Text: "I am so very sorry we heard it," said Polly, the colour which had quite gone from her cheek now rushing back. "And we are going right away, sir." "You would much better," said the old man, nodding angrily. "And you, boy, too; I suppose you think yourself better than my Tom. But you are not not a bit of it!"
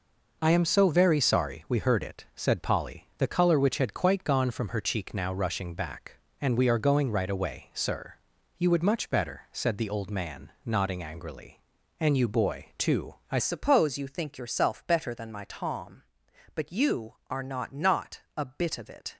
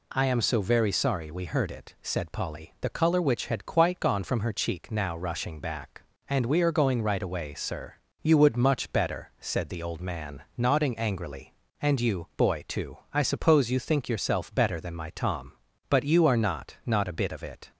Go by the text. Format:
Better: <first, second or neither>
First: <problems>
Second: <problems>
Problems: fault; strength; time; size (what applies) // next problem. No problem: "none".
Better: second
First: changes voice at "suppose"; from 13.3 s on; 5.8 s long // pauses between "not" and "a"; slight; at 18.2 s; 0.16 s long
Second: none